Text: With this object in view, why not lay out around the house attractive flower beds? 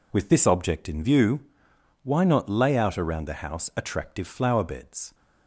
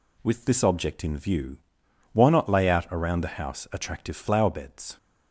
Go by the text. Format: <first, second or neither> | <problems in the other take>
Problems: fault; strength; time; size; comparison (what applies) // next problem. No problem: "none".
neither | none